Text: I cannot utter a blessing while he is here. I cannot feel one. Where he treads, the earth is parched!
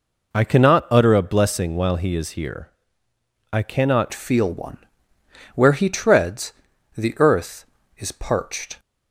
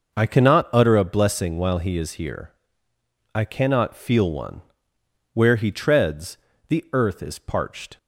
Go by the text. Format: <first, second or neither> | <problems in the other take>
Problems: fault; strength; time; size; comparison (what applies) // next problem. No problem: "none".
second | changes voice at "feel"; from 4.1 s on; 4.6 s long